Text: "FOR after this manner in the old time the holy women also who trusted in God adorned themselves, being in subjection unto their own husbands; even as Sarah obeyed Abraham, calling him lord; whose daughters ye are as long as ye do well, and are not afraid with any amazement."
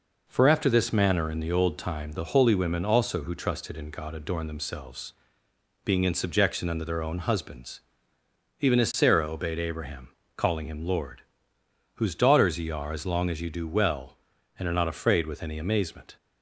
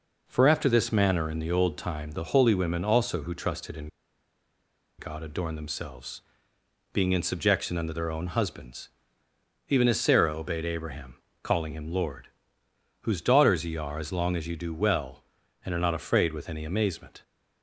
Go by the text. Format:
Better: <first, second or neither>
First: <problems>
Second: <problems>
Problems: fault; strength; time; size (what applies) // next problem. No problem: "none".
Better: first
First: none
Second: pauses between "in" and "God"; at 3.8 s; 1.1 s long